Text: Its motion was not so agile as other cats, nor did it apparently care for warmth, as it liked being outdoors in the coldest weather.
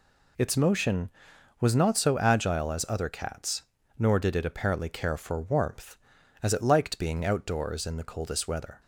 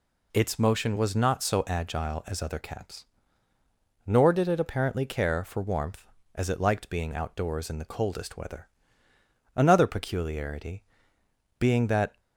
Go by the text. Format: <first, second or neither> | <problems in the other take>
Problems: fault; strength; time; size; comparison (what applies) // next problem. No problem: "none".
first | goes on to say "Another peculiarity being that"; strong; from 9.5 s on; 2.6 s long